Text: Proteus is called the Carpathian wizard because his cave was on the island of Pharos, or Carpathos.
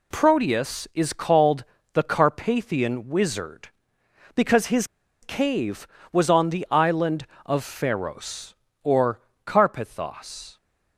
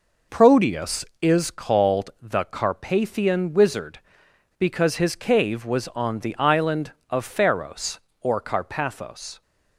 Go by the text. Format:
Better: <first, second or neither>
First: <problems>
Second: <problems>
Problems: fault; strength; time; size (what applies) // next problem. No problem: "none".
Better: second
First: pauses between "called" and "the"; slight; at 1.6 s; 0.30 s long // pauses between "his" and "cave"; at 4.8 s; 0.36 s long // pauses between "or" and "Carpathos"; slight; at 9.2 s; 0.24 s long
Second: none